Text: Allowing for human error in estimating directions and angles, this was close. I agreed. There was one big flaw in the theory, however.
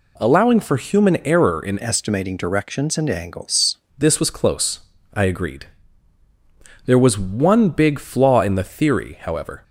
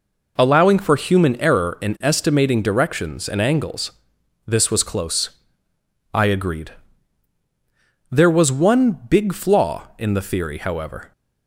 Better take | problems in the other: second | changes voice from "estimating" to "angles"; from 1.8 to 3.7 s; 1.9 s long

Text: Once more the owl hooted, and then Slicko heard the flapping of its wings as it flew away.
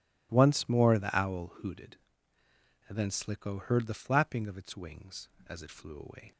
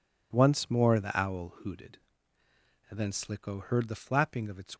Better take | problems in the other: first | stops before "wings as it flew away"; at 4.7 s

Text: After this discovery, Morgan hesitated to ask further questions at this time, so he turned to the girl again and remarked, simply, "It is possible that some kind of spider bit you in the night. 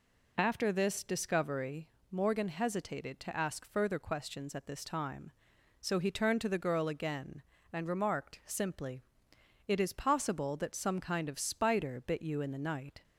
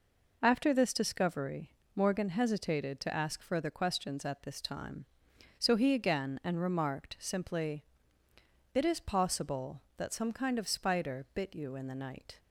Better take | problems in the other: first | skips "turned to the girl"; at 5.9 s

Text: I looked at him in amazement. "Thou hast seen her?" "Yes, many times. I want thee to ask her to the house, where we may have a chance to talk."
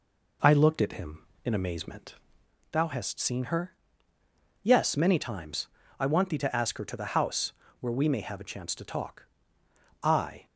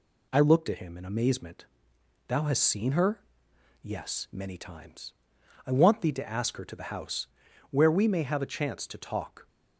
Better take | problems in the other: second | goes on to say "I"; slight; from 10.0 s on; 0.44 s long

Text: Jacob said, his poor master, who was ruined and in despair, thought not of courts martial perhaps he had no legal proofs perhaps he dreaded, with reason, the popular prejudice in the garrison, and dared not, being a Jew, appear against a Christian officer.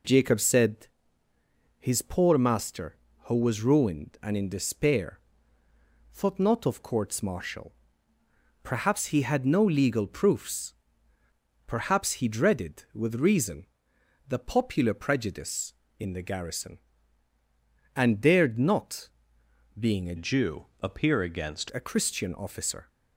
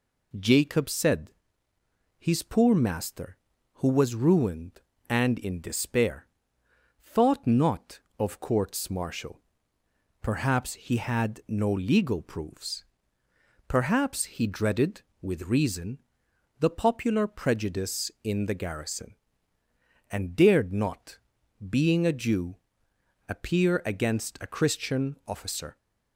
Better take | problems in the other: second | pauses between "martial" and "perhaps"; noticeable; at 7.7 s; 0.90 s long; noticeable in the second // pauses between "proofs" and "perhaps"; noticeable; at 10.7 s; 0.94 s long; noticeable in the second // changes voice from "Jew" to "against"; from 20.1 to 21.6 s; 1.5 s long

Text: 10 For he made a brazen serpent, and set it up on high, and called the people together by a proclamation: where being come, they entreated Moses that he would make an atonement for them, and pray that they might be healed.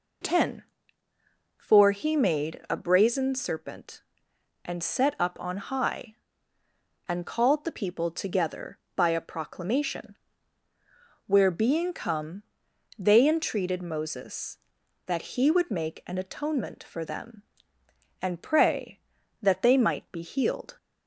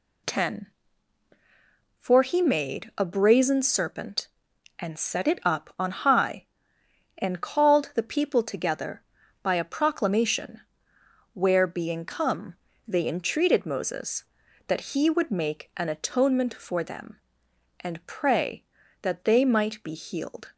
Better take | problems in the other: second | skips "it"; at 5.1 s

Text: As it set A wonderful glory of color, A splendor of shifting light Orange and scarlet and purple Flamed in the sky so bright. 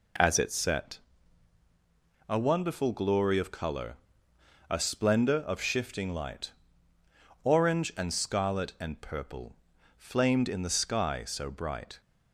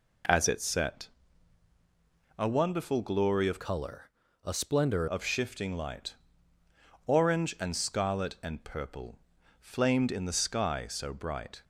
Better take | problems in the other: first | pauses between "set" and "A"; strong; at 1.0 s; 1.2 s long; strong in the first // changes voice from "color" to "splendor"; from 3.6 to 5.0 s; 1.4 s long // pauses between "light" and "Orange"; noticeable; at 6.1 s; 0.94 s long; noticeable in the first // pauses between "purple" and "Flamed"; at 9.1 s; 0.42 s long; also in the first

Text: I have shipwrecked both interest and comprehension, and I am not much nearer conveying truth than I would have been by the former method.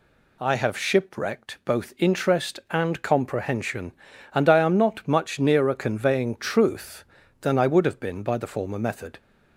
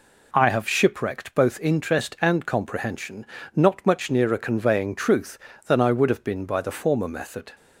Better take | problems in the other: first | skips "and I am"; at 3.3 s

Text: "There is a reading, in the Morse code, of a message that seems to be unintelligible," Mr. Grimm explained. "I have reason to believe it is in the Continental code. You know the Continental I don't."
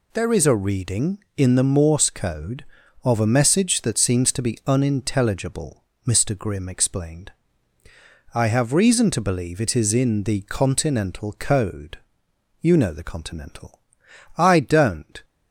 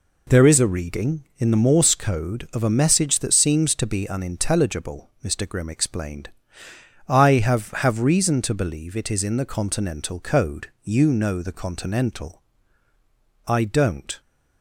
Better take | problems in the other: first | says "have" twice; at 7.7 s // pauses between "Continental" and "I"; at 12.4 s; 1.0 s long; noticeable in the first

